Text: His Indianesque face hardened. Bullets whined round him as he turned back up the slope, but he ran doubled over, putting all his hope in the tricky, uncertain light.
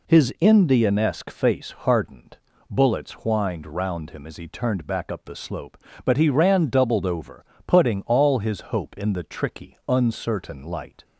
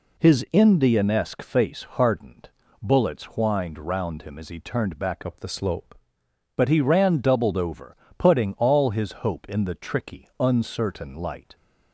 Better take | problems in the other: first | changes voice from "up" to "slope"; from 5.2 to 5.9 s; 0.7 s long

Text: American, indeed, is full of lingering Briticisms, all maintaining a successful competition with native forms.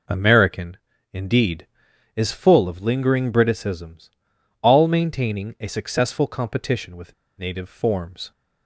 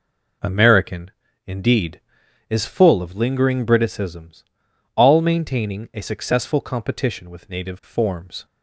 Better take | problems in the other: second | pauses between "with" and "native"; slight; at 7.1 s; 0.25 s long

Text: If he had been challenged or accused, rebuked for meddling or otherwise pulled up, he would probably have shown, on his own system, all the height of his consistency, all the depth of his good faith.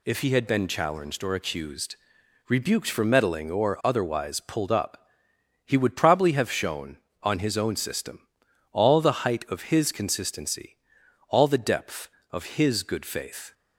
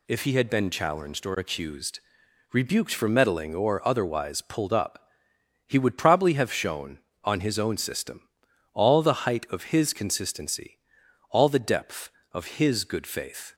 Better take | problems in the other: neither | none

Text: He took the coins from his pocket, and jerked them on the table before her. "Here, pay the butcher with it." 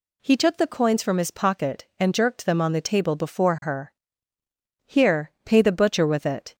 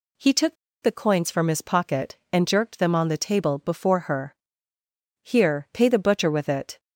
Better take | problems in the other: first | pauses between "took" and "the"; slight; at 0.5 s; 0.27 s long

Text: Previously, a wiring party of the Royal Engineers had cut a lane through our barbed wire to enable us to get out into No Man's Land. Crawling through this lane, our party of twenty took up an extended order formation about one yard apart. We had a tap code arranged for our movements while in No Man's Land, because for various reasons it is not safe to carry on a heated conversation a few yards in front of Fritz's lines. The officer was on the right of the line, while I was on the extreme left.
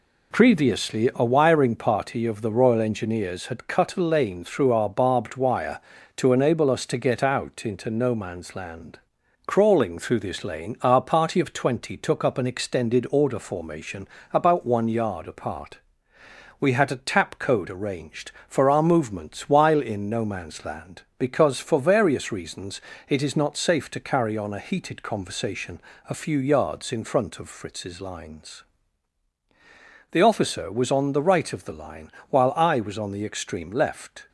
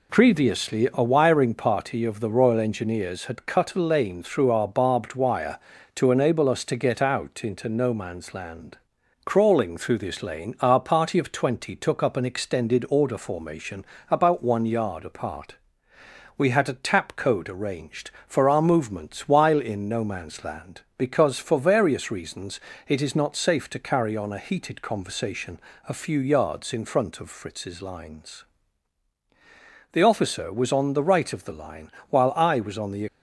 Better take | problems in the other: first | pauses between "formation" and "about"; slight; at 13.8 s; 0.24 s long; slight in the first // pauses between "reasons" and "it"; slight; at 22.5 s; 0.28 s long; slight in the first // pauses between "conversation" and "a"; slight; at 25.5 s; 0.28 s long; slight in the first // stops before "extreme left"; at 33.0 s

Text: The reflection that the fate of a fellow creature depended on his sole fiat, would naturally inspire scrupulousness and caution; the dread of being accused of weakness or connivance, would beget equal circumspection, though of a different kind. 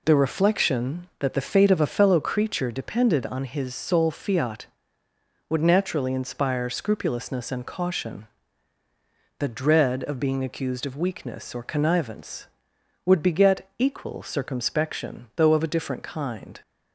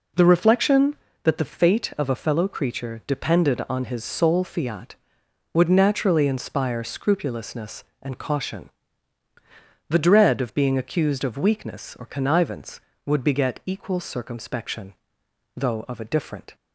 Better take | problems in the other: first | stops before "kind"; at 16.5 s

